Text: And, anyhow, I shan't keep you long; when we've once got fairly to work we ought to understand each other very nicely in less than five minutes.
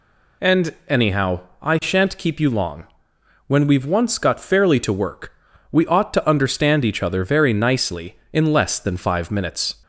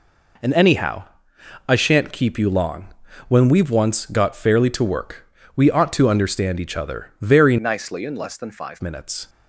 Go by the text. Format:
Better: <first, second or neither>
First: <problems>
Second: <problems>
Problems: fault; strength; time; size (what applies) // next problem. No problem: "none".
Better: first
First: pauses between "work" and "we"; at 5.3 s; 0.38 s long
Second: pauses between "work" and "we"; slight; at 5.2 s; 0.32 s long // changes voice from "nicely" to "five"; from 7.5 to 8.8 s; 1.3 s long